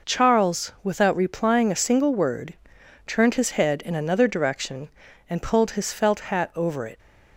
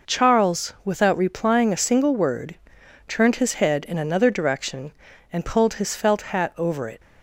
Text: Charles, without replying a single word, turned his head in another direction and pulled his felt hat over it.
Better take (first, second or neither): neither